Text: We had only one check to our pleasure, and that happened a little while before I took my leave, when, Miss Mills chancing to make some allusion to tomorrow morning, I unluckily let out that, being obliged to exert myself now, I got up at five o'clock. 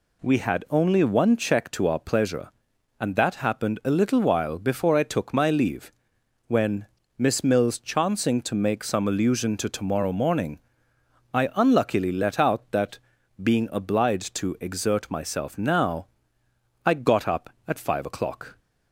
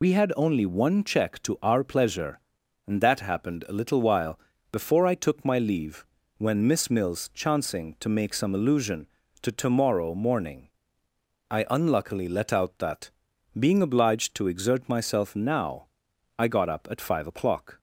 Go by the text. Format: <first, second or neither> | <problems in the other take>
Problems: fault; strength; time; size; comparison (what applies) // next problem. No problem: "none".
first | loses the start of "We"; at 0.0 s; 50 ms // pauses between "while" and "before"; slight; at 4.3 s; 0.32 s long